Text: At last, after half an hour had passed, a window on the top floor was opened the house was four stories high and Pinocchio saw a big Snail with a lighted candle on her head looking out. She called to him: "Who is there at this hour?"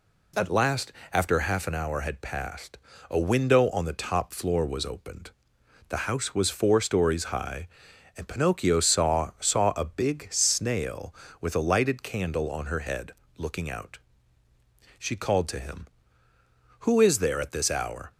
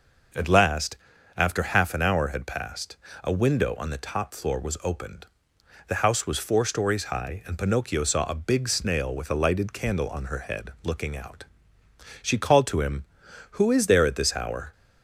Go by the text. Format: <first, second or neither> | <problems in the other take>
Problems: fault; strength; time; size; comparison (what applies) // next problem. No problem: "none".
second | pauses between "opened" and "the"; noticeable; at 5.3 s; 0.60 s long; noticeable in the second // says "saw" twice; at 9.4 s // pauses between "head" and "looking"; slight; at 13.1 s; 0.26 s long